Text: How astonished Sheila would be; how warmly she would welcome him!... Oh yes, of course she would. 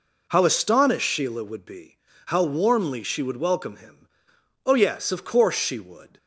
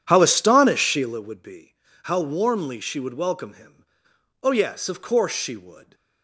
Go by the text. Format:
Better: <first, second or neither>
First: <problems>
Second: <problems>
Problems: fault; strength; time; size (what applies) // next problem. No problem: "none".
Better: first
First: none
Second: starts louder than the rest; strong; until 1.2 s; 9.5 dB